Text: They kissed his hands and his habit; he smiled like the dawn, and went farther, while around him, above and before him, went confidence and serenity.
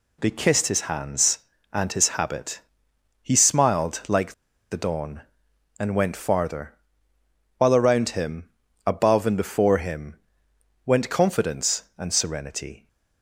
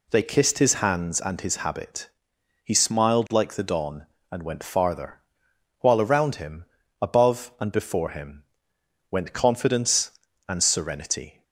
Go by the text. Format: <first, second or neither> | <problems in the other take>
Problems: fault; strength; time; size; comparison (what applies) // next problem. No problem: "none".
second | pauses between "like" and "the"; at 4.3 s; 0.37 s long